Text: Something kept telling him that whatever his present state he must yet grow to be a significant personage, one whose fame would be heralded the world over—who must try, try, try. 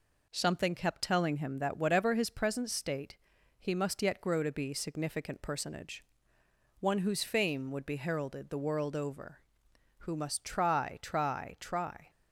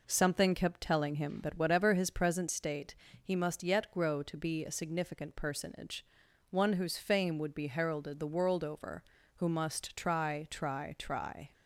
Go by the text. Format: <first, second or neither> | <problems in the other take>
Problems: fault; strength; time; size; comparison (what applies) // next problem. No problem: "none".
second | pauses between "state" and "he"; at 3.1 s; 0.44 s long; slight in the second // skips "a"; at 4.7 s